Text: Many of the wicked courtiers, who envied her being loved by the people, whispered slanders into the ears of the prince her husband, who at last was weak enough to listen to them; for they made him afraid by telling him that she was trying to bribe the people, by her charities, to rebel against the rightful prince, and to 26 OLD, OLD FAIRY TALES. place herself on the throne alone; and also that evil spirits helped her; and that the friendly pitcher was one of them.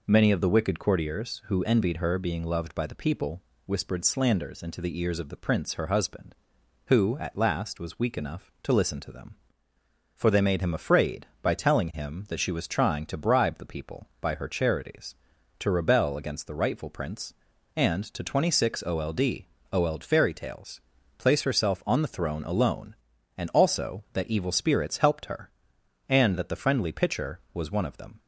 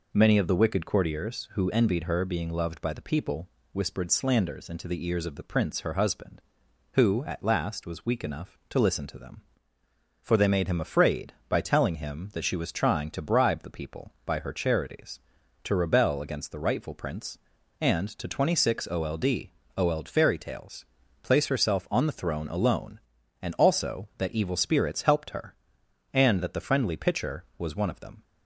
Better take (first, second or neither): neither